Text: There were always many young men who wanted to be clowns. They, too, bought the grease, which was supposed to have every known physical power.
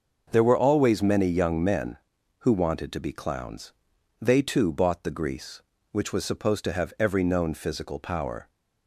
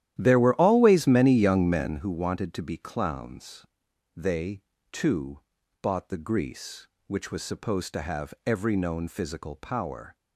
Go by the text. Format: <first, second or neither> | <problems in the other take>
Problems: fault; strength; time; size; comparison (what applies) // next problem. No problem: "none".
first | starts louder than the rest; strong; until 2.0 s; 12 dB